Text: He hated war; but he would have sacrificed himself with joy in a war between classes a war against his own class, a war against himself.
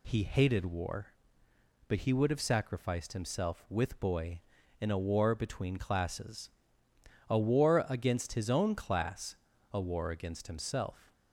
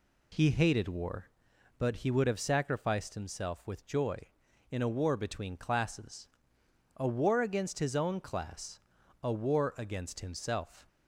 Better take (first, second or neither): second